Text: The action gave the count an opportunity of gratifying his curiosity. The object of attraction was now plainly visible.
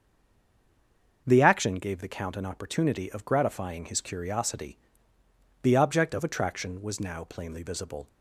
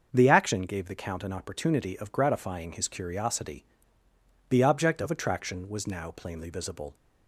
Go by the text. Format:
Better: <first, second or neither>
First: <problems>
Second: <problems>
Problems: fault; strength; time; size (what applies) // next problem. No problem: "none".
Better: second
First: stays silent before the first word; noticeable; until 1.2 s; 1.2 s long // starts louder than the rest; until 2.2 s; 6 dB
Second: starts louder than the rest; until 1.1 s; 6 dB